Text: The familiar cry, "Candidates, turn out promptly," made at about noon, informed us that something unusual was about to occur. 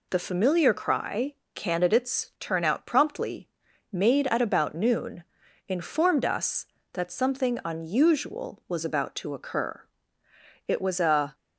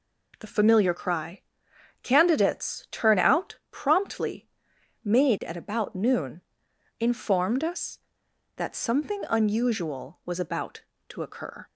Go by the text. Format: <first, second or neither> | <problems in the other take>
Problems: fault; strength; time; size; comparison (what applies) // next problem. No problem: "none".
second | goes on to say "It was a"; noticeable; from 10.6 s on; 0.66 s long